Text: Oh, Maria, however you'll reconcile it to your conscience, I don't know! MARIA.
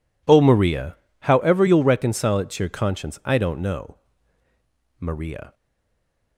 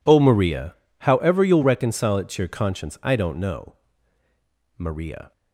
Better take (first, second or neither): second